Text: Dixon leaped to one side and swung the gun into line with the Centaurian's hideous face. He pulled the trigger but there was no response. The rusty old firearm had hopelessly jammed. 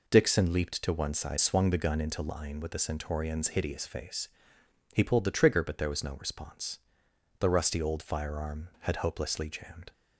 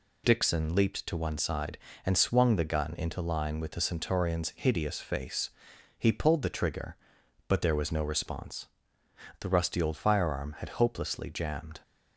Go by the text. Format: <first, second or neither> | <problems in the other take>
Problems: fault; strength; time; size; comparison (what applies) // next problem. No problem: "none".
second | skips "and"; at 1.3 s